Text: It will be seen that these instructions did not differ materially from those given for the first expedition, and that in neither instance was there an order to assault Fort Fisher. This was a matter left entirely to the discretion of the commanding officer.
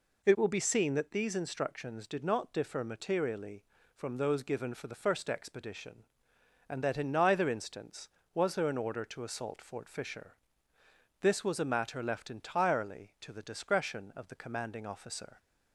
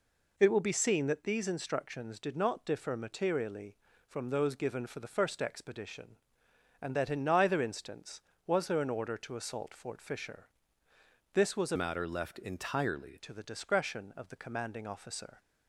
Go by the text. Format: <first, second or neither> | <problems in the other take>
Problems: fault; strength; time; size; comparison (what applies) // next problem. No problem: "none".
first | changes voice from "matter" to "entirely"; from 11.7 to 13.1 s; 1.4 s long